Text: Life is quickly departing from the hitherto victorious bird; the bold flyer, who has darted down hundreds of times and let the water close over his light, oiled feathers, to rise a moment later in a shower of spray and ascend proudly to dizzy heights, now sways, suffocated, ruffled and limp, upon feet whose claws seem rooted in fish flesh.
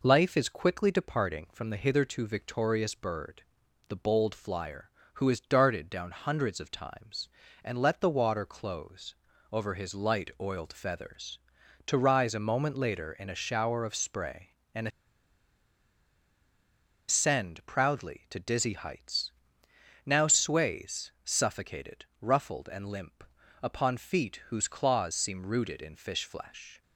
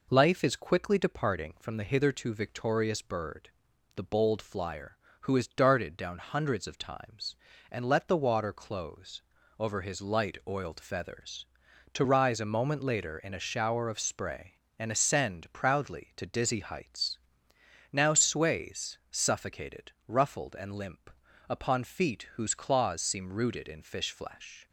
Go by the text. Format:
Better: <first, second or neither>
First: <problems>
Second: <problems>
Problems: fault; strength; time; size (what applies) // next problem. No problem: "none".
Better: second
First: pauses between "close" and "over"; at 9.1 s; 0.38 s long // pauses between "and" and "ascend"; strong; at 14.8 s; 2.2 s long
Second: pauses between "close" and "over"; at 9.2 s; 0.38 s long